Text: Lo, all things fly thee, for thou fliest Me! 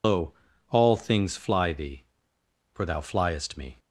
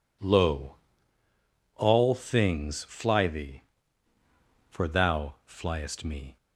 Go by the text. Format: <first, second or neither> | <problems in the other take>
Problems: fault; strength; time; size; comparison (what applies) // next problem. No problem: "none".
second | loses the start of "Lo"; at 0.0 s; 75 ms